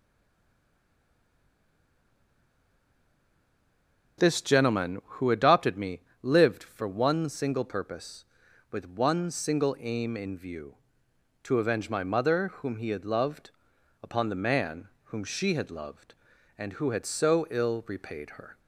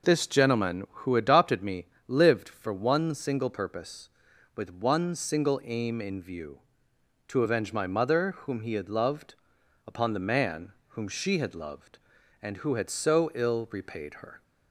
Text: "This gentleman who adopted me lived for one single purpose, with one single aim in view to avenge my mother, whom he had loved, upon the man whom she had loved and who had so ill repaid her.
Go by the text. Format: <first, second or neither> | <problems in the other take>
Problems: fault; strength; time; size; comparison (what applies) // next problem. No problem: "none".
second | stays silent before the first word; strong; until 4.1 s; 4.1 s long // pauses between "me" and "lived"; slight; at 6.0 s; 0.20 s long; slight in the second // pauses between "man" and "whom"; slight; at 14.8 s; 0.16 s long; slight in the second